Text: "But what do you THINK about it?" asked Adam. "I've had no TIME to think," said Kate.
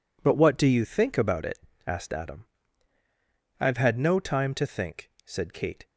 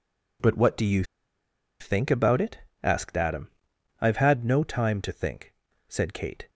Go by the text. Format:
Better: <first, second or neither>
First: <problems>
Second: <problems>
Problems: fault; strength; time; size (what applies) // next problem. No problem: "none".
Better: first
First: none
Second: pauses between "you" and "THINK"; noticeable; at 1.0 s; 0.77 s long